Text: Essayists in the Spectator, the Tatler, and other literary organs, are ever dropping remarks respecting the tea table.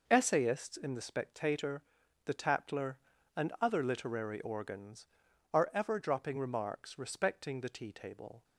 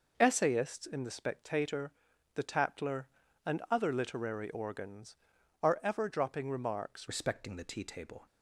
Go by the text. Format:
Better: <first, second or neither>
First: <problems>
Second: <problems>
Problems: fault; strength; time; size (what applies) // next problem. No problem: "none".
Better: first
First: none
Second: changes voice at "respecting"; from 7.0 s on; 1.2 s long